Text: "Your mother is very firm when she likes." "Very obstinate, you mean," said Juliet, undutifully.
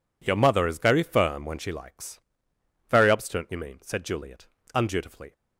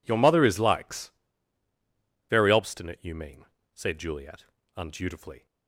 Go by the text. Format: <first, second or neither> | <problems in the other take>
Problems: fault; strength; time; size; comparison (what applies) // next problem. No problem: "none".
first | skips "very firm when she"; at 0.5 s